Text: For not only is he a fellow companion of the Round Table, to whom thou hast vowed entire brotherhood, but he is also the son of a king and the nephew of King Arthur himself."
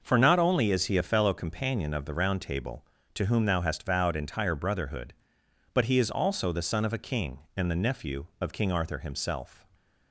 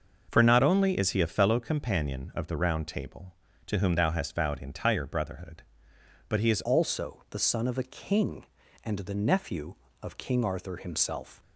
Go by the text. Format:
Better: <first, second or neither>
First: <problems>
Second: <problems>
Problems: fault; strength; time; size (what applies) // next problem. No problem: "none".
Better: first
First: starts louder than the rest; noticeable; until 1.0 s; 6 dB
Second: starts louder than the rest; until 1.3 s; 6 dB // changes voice at "also"; from 6.6 s on; 4.8 s long